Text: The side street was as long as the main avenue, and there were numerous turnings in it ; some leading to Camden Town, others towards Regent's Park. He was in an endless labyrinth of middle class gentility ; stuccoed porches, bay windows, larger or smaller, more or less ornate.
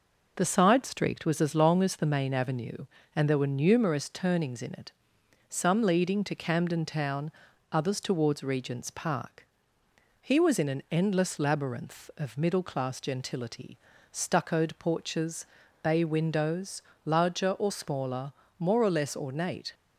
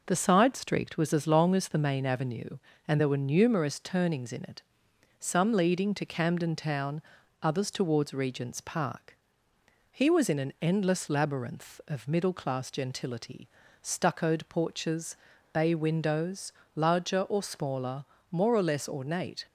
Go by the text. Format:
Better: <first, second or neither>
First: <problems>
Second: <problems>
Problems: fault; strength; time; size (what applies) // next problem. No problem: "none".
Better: neither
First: none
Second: none